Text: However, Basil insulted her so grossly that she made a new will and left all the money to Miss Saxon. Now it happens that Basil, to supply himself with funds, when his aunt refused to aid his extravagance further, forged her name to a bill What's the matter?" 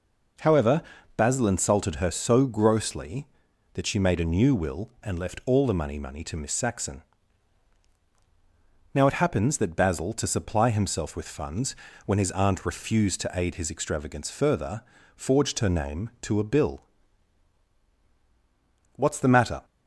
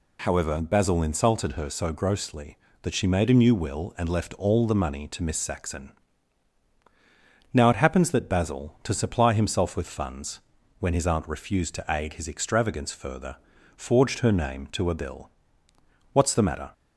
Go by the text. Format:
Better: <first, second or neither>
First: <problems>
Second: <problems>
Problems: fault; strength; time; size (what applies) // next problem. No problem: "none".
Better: second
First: says "money" twice; at 5.9 s // pauses between "bill" and "What's"; strong; at 16.8 s; 2.1 s long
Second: pauses between "bill" and "What's"; noticeable; at 15.3 s; 0.82 s long